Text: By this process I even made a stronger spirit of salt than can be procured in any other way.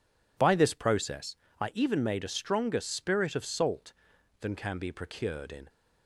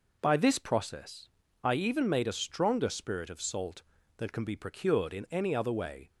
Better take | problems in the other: second | pauses between "process" and "I"; slight; at 1.3 s; 0.24 s long; slight in the second // stops before "any other way"; at 5.6 s

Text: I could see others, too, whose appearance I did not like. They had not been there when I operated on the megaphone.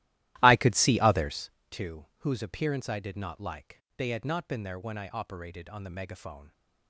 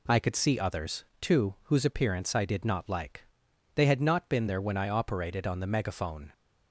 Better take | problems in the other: second | starts louder than the rest; strong; until 1.6 s; 15.5 dB

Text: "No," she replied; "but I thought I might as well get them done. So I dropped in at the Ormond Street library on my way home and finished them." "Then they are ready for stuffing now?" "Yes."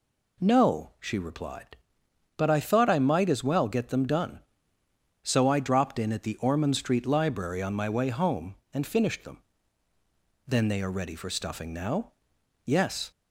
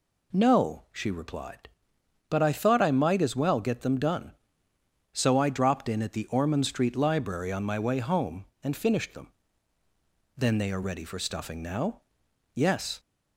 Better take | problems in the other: neither | none

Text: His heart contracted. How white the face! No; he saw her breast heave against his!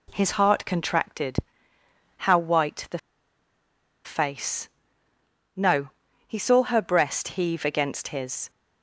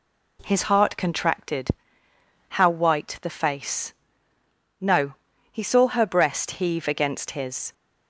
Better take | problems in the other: second | pauses between "the" and "face"; at 2.9 s; 1.0 s long

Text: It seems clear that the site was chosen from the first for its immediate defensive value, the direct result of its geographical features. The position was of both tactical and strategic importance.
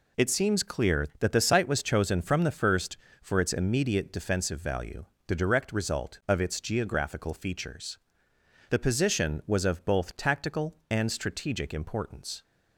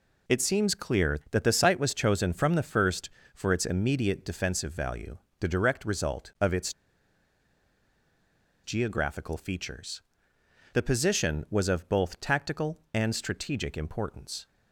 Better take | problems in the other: first | pauses between "its" and "geographical"; strong; at 6.7 s; 1.9 s long

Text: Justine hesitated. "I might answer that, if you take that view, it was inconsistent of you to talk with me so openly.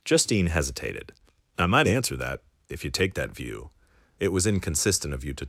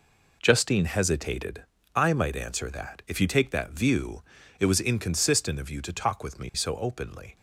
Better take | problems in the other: second | stops before "talk with me so openly"; at 5.4 s

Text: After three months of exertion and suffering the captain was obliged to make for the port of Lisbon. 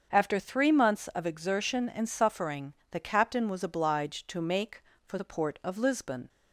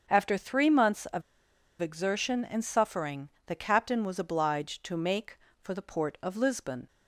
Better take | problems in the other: first | starts louder than the rest; until 1.1 s; 7 dB; also in the first // pauses between "of" and "exertion"; noticeable; at 1.2 s; 0.59 s long // pauses between "suffering" and "the"; slight; at 3.2 s; 0.18 s long; slight in the first

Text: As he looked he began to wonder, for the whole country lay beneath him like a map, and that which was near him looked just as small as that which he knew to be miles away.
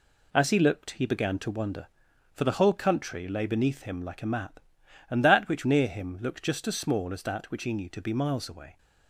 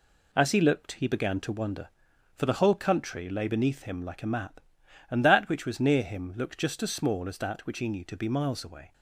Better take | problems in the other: second | skips "was"; at 5.6 s

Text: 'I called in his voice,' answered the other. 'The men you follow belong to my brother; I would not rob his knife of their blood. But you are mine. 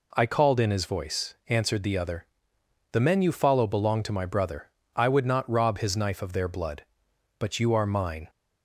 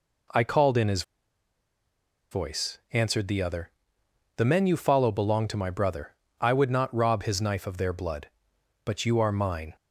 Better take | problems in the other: first | pauses between "his" and "voice"; strong; at 1.0 s; 1.2 s long

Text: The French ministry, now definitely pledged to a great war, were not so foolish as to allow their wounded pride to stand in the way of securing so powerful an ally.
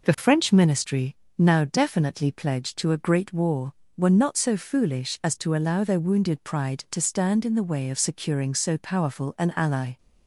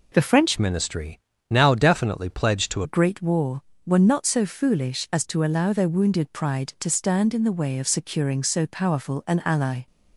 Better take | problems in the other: first | changes voice from "ministry" to "to"; from 0.5 to 2.8 s; 2.3 s long

